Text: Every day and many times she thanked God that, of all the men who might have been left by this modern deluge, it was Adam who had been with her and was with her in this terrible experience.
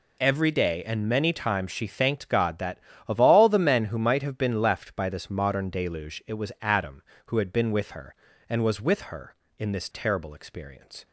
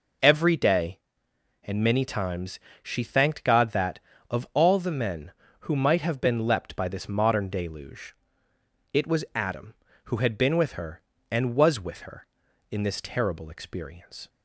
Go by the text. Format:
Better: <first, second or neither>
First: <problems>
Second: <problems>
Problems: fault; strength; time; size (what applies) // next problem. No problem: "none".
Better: first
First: none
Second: pauses between "times" and "she"; slight; at 2.5 s; 0.24 s long // says "leapt" for "left"; at 6.4 s